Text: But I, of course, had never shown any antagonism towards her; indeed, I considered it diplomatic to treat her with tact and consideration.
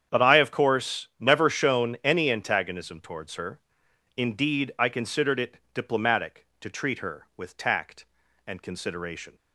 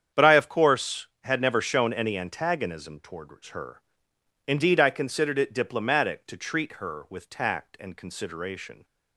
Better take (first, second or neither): second